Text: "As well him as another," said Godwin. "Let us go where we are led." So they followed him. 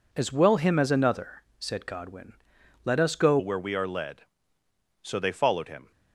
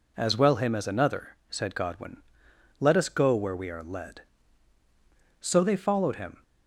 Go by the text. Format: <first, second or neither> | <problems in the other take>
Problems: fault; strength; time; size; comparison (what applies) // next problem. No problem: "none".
second | changes voice at "where"; from 3.3 s on; 2.6 s long